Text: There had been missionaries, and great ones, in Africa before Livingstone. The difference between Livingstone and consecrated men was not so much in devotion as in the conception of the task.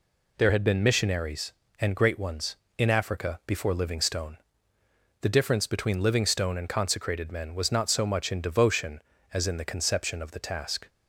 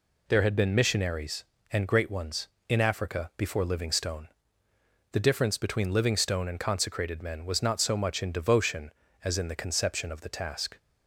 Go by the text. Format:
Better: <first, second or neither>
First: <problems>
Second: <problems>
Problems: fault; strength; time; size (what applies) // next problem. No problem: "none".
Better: neither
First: none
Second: none